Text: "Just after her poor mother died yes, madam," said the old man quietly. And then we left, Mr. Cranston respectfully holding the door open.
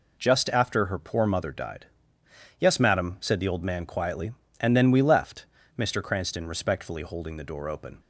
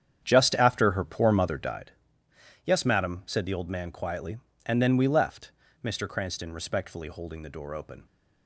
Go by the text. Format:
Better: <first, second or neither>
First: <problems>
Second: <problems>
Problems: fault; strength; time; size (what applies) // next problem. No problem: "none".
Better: first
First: pauses between "died" and "yes"; noticeable; at 1.8 s; 0.74 s long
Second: starts louder than the rest; strong; until 1.9 s; 8.5 dB // pauses between "died" and "yes"; noticeable; at 1.9 s; 0.74 s long